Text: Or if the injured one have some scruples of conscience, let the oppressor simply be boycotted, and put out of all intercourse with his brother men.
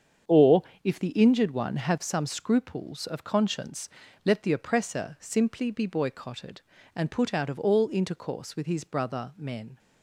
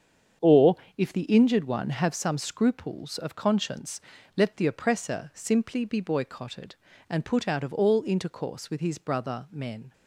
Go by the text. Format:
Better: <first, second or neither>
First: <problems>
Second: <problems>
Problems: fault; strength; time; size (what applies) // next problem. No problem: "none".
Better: neither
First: starts louder than the rest; strong; until 1.4 s; 7.5 dB // pauses between "Or" and "if"; slight; at 0.6 s; 0.20 s long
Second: starts louder than the rest; strong; until 1.6 s; 7.5 dB // pauses between "Or" and "if"; slight; at 0.7 s; 0.20 s long